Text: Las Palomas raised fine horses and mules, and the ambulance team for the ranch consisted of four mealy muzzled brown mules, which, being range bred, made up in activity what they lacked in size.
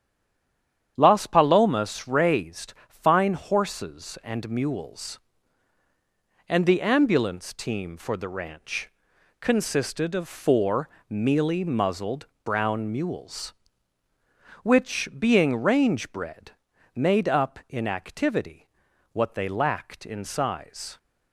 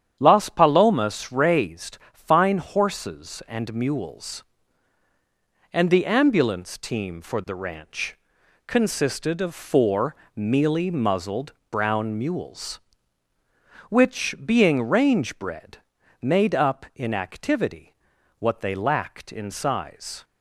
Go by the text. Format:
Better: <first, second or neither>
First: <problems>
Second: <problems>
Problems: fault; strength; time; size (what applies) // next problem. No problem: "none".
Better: second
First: stays silent before the first word; slight; until 0.9 s; 0.9 s long // starts louder than the rest; strong; until 1.9 s; 9 dB // pauses between "ranch" and "consisted"; noticeable; at 8.8 s; 0.50 s long // pauses between "four" and "mealy"; slight; at 10.8 s; 0.18 s long // pauses between "muzzled" and "brown"; slight; at 12.2 s; 0.18 s long // pauses between "activity" and "what"; noticeable; at 18.6 s; 0.46 s long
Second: starts louder than the rest; strong; until 1.2 s; 9 dB // pauses between "ranch" and "consisted"; noticeable; at 8.1 s; 0.50 s long // pauses between "four" and "mealy"; slight; at 10.1 s; 0.18 s long // pauses between "muzzled" and "brown"; slight; at 11.5 s; 0.18 s long // pauses between "activity" and "what"; noticeable; at 17.9 s; 0.46 s long